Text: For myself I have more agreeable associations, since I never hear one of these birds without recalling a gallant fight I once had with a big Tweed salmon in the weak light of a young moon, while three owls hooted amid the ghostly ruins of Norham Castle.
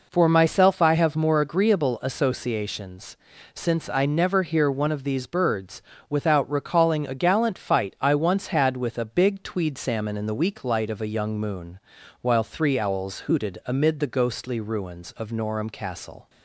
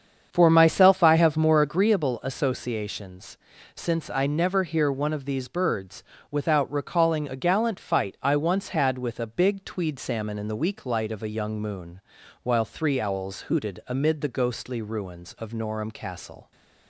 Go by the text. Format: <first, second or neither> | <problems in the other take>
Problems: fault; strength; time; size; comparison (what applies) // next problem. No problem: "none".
first | starts louder than the rest; strong; until 1.9 s; 7.5 dB // pauses between "birds" and "without"; slight; at 6.0 s; 0.26 s long; slight in the first